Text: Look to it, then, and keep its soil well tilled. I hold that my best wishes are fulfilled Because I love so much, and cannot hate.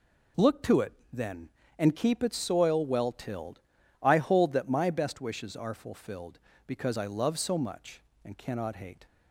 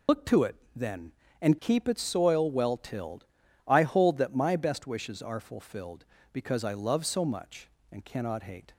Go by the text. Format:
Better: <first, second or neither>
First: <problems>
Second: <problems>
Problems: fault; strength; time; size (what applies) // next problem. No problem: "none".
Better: first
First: none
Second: loses the start of "Look"; at 0.0 s; 105 ms